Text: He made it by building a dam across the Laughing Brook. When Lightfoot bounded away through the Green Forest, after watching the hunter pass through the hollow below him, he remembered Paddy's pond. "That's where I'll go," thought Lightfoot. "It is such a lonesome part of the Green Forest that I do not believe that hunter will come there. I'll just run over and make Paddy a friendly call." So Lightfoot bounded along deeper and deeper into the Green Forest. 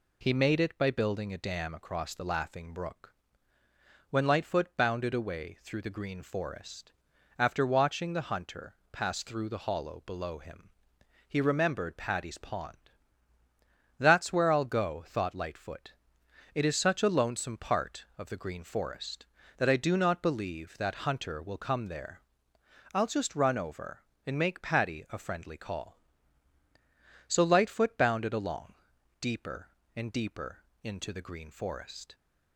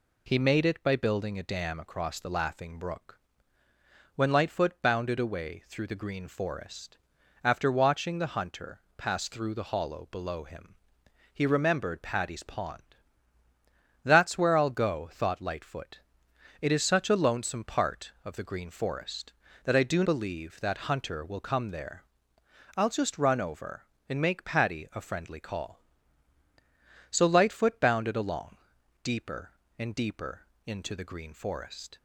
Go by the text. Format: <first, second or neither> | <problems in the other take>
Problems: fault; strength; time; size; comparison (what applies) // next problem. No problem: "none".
first | pauses between "hunter" and "pass"; slight; at 8.8 s; 0.16 s long; slight in the first // skips "not"; at 20.0 s // pauses between "along" and "deeper"; noticeable; at 28.5 s; 0.46 s long; noticeable in the first // pauses between "deeper" and "into"; slight; at 30.4 s; 0.22 s long; slight in the first